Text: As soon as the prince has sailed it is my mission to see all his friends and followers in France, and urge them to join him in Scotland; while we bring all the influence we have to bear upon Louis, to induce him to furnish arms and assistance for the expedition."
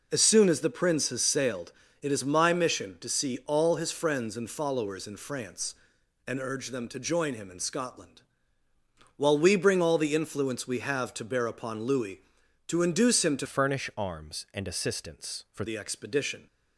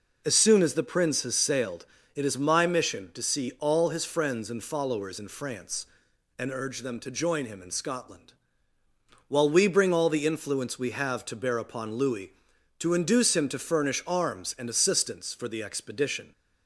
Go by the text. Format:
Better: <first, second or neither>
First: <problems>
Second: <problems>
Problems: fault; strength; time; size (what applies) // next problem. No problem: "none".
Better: second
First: pauses between "sailed" and "it"; slight; at 1.7 s; 0.28 s long // changes voice from "furnish" to "for"; from 13.4 to 15.6 s; 2.2 s long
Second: pauses between "sailed" and "it"; slight; at 1.8 s; 0.28 s long